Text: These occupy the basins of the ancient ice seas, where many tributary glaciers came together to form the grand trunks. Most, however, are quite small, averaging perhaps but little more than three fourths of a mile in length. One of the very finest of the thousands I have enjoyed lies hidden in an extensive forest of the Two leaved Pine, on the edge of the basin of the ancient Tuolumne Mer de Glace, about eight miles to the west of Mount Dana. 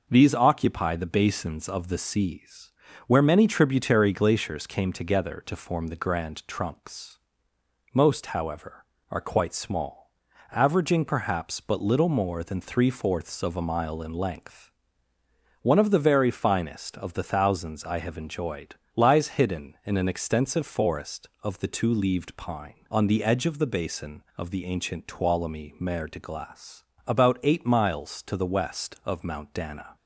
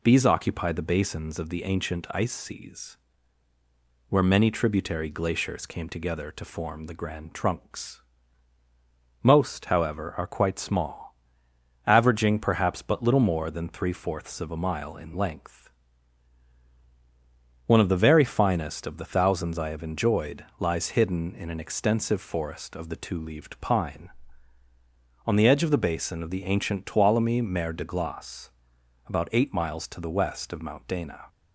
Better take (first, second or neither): second